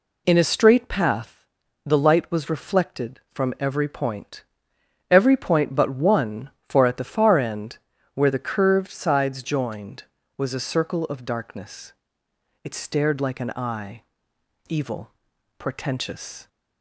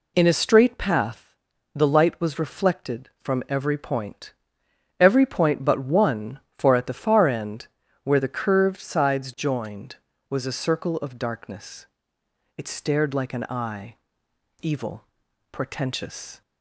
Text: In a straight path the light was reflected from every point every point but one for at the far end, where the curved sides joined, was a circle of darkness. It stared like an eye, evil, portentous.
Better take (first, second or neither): neither